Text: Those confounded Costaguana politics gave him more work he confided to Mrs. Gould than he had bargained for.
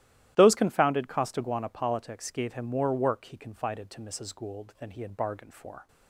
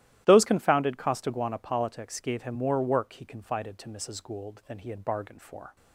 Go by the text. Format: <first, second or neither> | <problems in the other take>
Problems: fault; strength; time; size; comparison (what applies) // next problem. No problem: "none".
neither | starts louder than the rest; strong; the same in both